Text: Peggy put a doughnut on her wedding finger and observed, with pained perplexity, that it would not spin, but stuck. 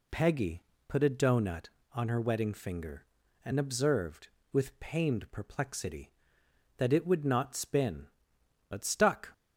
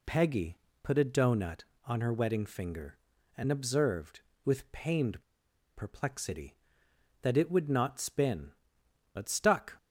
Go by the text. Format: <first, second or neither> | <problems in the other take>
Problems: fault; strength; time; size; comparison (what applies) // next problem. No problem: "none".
first | pauses between "Peggy" and "put"; slight; at 0.5 s; 0.24 s long; slight in the first // pauses between "pained" and "perplexity"; noticeable; at 5.2 s; 0.52 s long